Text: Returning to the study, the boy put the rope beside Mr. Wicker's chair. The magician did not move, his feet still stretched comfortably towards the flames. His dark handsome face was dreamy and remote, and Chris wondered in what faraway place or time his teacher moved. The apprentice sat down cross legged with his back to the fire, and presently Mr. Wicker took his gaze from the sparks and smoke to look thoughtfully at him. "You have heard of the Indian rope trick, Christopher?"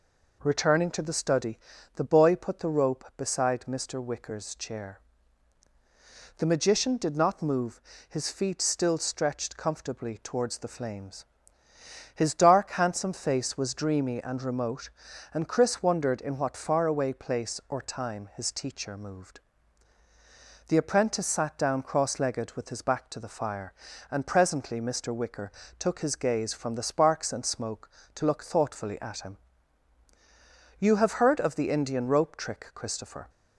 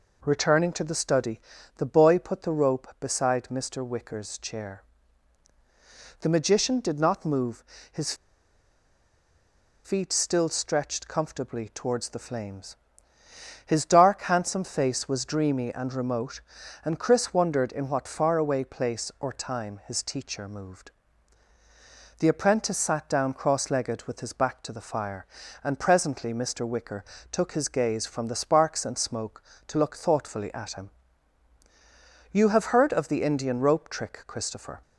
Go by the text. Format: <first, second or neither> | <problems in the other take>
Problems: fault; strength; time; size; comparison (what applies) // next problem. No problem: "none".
first | pauses between "his" and "feet"; strong; at 8.1 s; 1.7 s long // pauses between "Wicker" and "took"; slight; at 27.0 s; 0.28 s long; slight in the first